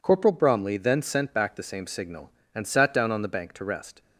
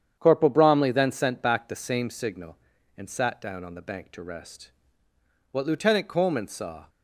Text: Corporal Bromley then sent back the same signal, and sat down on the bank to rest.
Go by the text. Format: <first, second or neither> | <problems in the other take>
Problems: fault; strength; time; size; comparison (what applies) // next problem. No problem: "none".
first | starts louder than the rest; strong; until 1.1 s; 8.5 dB // goes on to say "What Lieutenant Coleman saw"; from 5.5 s on; 1.3 s long